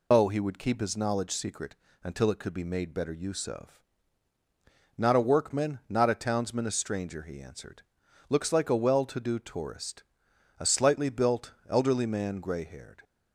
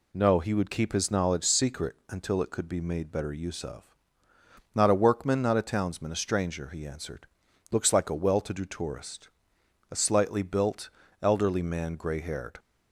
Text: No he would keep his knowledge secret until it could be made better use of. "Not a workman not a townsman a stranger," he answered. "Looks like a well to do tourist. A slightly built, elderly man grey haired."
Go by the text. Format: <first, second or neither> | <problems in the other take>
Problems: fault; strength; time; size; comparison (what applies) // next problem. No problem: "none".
second | loses the start of "No"; at 0.1 s; 135 ms // pauses between "secret" and "until"; slight; at 1.7 s; 0.28 s long